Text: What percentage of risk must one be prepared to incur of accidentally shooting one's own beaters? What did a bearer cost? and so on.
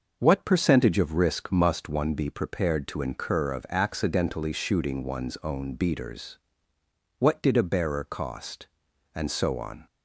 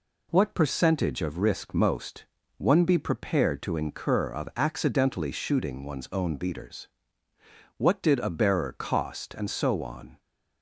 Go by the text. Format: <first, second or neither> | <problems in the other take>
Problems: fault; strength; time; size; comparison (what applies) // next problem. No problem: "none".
first | says "most" for "must"; at 1.7 s